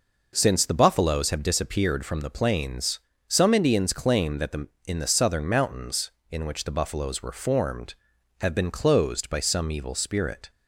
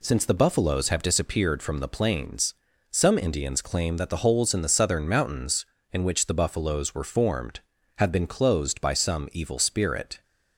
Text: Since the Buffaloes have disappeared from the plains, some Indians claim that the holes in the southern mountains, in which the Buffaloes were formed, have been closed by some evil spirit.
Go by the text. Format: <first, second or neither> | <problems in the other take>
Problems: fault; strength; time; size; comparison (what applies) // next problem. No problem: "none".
second | skips "holes"; at 4.7 s